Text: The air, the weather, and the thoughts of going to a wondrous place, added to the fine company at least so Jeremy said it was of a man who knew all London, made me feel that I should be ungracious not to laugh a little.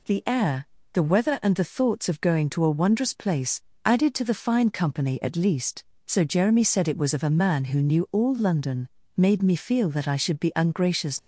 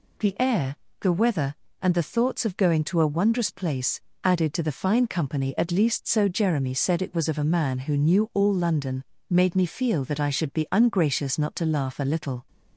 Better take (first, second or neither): second